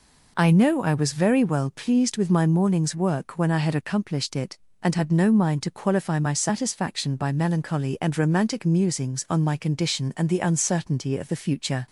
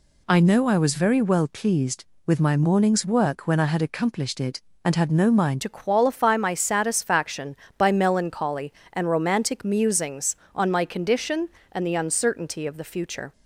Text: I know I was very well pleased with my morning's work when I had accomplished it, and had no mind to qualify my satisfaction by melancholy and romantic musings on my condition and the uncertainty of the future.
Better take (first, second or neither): first